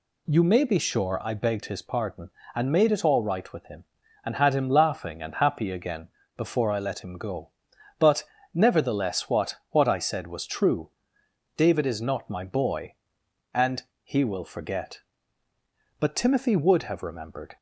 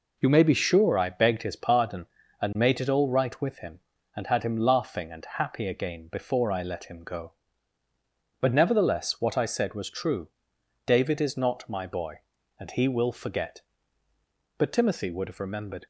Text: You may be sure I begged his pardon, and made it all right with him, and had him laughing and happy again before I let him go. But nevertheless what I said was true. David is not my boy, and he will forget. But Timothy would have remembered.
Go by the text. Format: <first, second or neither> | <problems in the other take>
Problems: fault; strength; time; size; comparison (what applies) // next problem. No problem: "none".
second | pauses between "again" and "before"; slight; at 6.0 s; 0.28 s long // pauses between "But" and "nevertheless"; slight; at 8.2 s; 0.32 s long // says "what" twice; at 9.7 s // pauses between "and" and "he"; slight; at 13.8 s; 0.20 s long